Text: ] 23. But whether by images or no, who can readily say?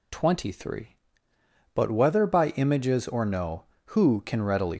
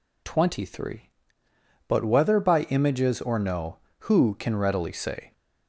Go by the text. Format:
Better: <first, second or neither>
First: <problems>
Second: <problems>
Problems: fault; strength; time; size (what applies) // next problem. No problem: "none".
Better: second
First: stops before "say"; at 4.7 s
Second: none